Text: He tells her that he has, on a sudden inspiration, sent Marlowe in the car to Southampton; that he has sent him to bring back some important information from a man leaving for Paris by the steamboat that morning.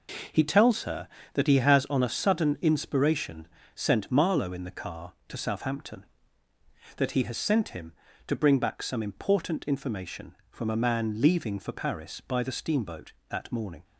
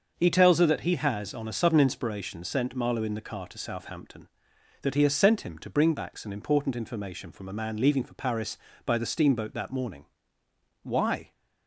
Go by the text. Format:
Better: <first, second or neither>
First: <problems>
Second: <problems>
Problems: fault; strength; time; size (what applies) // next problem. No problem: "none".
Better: first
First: none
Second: starts louder than the rest; until 1.1 s; 6.5 dB // goes on to say "Why"; slight; from 10.8 s on; 0.48 s long